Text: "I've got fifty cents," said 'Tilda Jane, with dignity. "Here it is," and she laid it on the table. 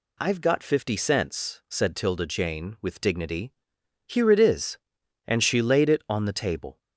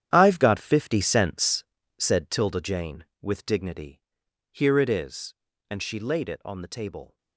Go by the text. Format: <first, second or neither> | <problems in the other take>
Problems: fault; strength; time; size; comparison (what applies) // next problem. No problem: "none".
first | gets quieter; strong; throughout; 12 dB